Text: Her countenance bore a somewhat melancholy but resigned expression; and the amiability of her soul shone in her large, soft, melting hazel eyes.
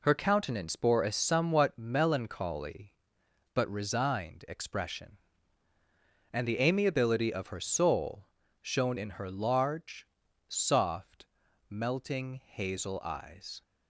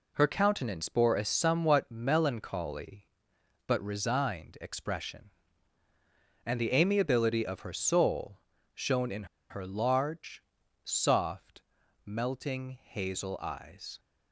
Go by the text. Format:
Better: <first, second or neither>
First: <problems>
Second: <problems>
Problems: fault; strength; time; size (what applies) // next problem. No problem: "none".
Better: first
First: pauses between "soul" and "shone"; slight; at 8.2 s; 0.36 s long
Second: pauses between "soul" and "shone"; slight; at 8.3 s; 0.36 s long // pauses between "in" and "her"; slight; at 9.2 s; 0.27 s long